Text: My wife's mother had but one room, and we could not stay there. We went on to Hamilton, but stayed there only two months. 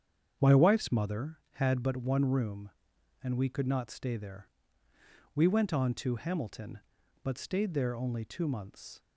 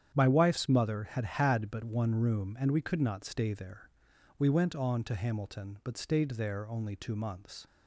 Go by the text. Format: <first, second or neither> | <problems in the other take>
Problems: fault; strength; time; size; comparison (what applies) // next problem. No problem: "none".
first | starts louder than the rest; strong; until 1.1 s; 9 dB; strong in the first // says "had" twice; at 1.2 s